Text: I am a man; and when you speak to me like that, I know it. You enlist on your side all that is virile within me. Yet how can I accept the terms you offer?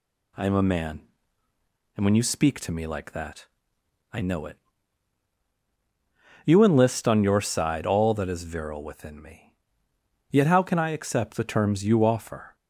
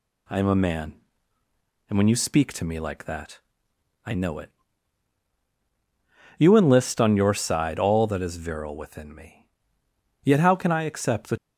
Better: first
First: none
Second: stops before "terms you offer"; at 11.3 s

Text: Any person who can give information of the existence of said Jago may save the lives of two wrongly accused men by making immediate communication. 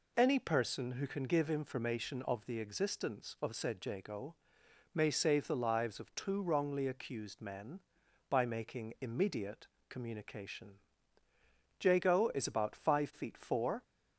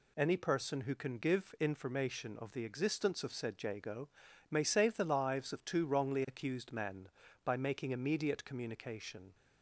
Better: second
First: pauses between "Jago" and "may"; noticeable; at 4.3 s; 0.56 s long // pauses between "immediate" and "communication"; slight; at 9.6 s; 0.22 s long // goes on to say "Jago is about five feet four"; strong; from 11.8 s on; 1.9 s long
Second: pauses between "Jago" and "may"; at 4.0 s; 0.40 s long

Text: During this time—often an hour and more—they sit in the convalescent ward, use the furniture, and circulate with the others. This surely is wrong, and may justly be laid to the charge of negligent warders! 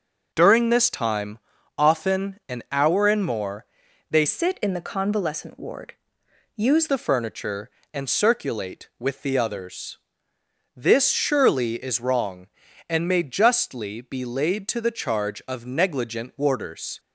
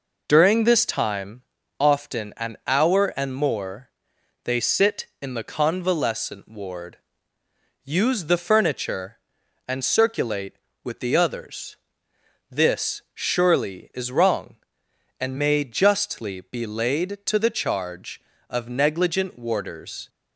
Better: second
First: changes voice from "sit" to "use"; from 4.2 to 6.8 s; 2.6 s long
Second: none

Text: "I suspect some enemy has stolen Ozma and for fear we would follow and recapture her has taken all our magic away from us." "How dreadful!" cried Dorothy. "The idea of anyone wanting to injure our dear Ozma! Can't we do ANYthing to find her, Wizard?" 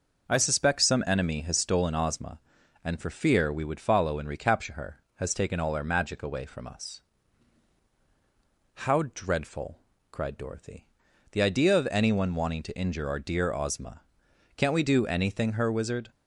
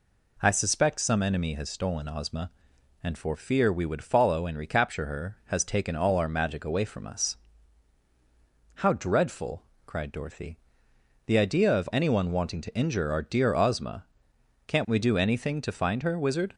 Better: second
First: skips "to find"; at 15.5 s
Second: none

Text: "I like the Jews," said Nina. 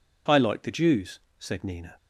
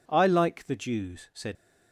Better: first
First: none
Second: stops before "Nina"; at 1.5 s

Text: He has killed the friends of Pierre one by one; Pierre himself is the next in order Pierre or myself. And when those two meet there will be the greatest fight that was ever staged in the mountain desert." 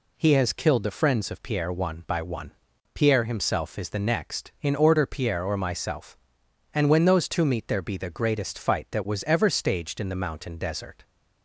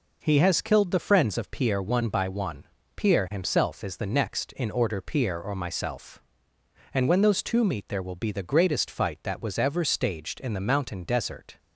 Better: second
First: skips "will"; at 7.8 s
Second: none

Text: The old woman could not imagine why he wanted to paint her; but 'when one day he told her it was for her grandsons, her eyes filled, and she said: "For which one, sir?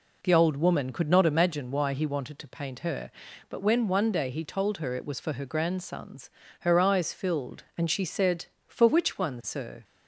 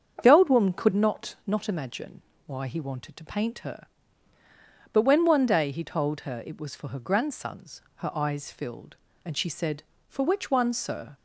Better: first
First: none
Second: starts louder than the rest; strong; until 1.2 s; 7 dB // says "not" twice; at 1.4 s // pauses between "imagine" and "why"; slight; at 2.2 s; 0.24 s long

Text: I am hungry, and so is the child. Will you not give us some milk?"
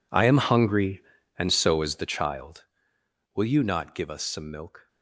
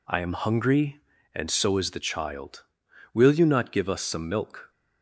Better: second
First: gets quieter; strong; throughout; 18.5 dB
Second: none

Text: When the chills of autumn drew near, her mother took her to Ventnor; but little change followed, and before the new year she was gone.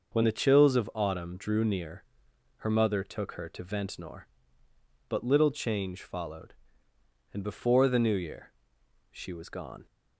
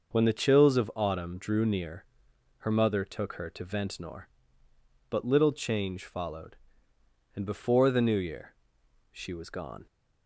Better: neither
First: pauses between "year" and "she"; noticeable; at 8.4 s; 0.62 s long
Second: pauses between "year" and "she"; noticeable; at 8.5 s; 0.60 s long

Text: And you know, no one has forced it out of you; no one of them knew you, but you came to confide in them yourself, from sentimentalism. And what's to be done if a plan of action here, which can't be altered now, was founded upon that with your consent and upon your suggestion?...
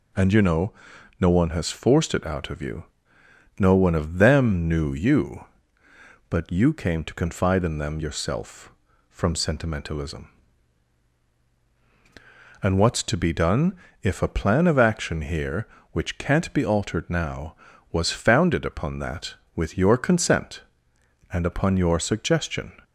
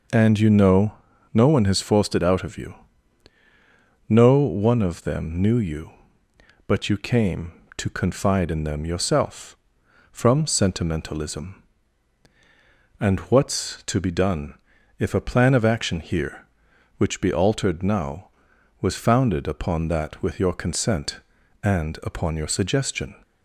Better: first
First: pauses between "done" and "if"; slight; at 13.7 s; 0.26 s long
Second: pauses between "done" and "if"; at 14.5 s; 0.44 s long // skips "can't"; at 17.2 s

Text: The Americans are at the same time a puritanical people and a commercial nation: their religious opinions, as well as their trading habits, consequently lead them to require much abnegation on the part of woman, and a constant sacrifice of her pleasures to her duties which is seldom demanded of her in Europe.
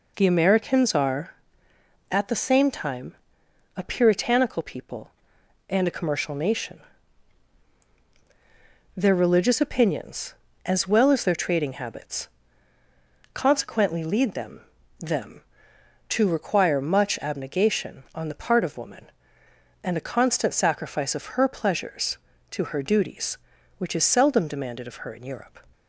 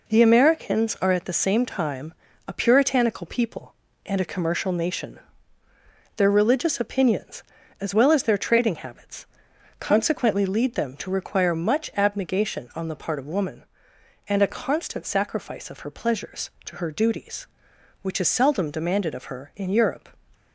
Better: second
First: pauses between "time" and "a"; noticeable; at 3.1 s; 0.58 s long // says "them" twice; at 14.9 s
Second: pauses between "time" and "a"; slight; at 2.1 s; 0.32 s long

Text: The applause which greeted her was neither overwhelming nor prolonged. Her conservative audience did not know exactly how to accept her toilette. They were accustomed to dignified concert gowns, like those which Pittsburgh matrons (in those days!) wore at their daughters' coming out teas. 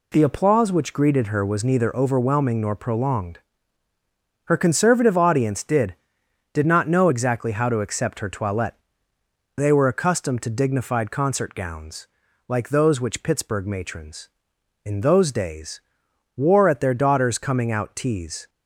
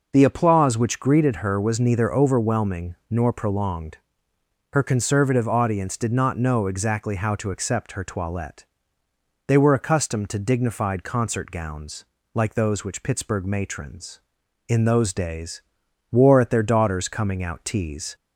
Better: second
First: says "did" twice; at 6.5 s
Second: none

